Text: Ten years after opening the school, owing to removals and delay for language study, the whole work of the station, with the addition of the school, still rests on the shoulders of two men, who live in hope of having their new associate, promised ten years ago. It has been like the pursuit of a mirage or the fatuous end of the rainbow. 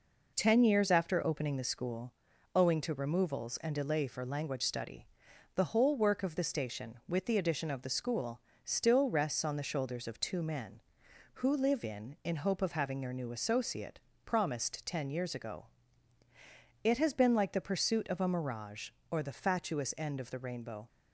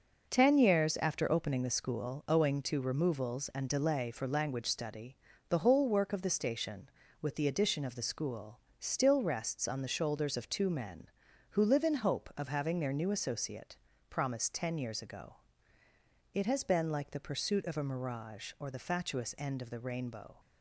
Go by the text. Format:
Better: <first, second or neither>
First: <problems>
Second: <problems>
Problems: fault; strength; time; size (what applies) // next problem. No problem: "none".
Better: second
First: says "in" twice; at 12.2 s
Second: none